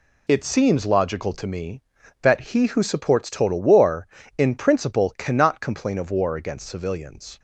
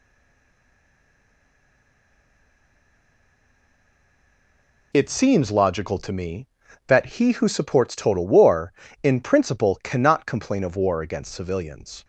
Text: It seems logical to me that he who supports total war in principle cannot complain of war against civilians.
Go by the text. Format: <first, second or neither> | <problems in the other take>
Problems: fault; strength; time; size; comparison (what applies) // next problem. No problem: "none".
first | stays silent before the first word; strong; until 4.9 s; 4.9 s long